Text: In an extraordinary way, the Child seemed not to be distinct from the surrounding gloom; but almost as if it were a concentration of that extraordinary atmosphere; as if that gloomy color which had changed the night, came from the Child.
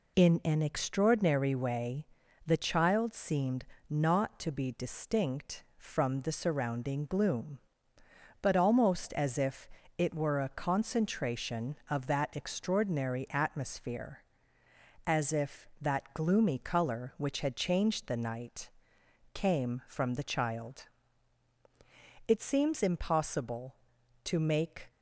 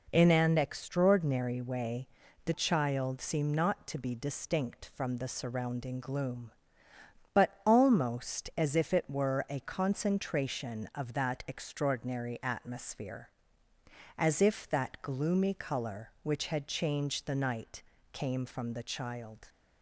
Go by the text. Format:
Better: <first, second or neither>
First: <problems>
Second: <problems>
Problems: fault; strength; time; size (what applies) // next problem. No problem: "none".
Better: second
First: pauses between "seemed" and "not"; slight; at 3.6 s; 0.26 s long // pauses between "if" and "it"; slight; at 9.6 s; 0.30 s long // goes on to say "It seems impossible to make"; strong; from 22.2 s on; 2.6 s long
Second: none